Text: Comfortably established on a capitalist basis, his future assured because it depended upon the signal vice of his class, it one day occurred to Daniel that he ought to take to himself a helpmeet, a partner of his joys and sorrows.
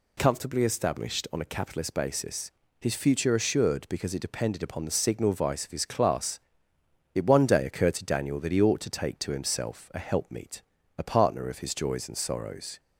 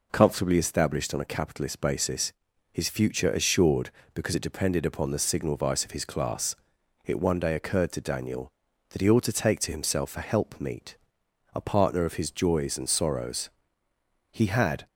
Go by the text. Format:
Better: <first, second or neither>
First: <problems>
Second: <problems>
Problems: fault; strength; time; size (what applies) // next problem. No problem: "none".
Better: first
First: none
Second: goes on to say "He had"; from 14.3 s on; 0.56 s long